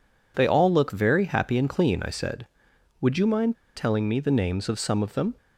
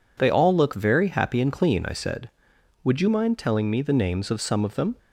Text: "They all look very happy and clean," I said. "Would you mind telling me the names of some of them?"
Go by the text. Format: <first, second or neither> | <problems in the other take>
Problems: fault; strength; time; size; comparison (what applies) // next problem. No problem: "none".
second | pauses between "mind" and "telling"; slight; at 3.5 s; 0.20 s long